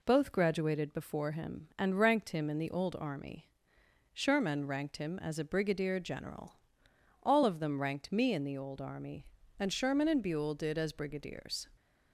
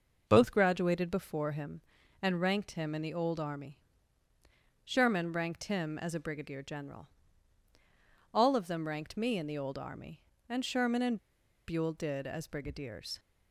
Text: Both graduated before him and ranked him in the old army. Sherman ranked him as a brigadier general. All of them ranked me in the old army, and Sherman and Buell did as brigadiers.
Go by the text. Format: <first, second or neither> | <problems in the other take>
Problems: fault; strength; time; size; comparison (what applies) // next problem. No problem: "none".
first | pauses between "and" and "Buell"; noticeable; at 11.1 s; 0.50 s long